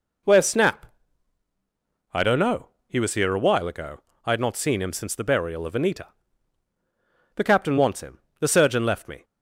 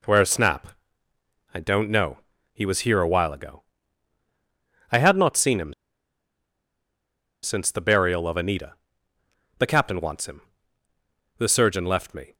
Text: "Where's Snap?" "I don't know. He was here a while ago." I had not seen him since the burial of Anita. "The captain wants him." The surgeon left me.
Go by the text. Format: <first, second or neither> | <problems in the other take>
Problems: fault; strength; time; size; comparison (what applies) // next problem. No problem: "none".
first | pauses between "him" and "since"; strong; at 5.7 s; 1.7 s long